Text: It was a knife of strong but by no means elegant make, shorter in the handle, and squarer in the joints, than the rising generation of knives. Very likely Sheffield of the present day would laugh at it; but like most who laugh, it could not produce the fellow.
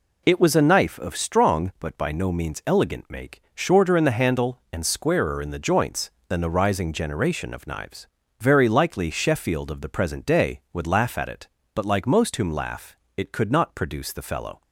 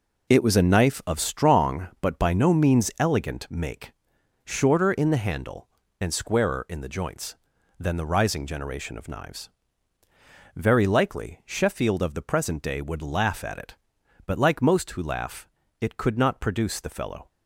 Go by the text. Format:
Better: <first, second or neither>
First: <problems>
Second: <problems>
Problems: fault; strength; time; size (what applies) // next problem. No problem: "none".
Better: second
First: says "whom" for "who"; at 12.3 s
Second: none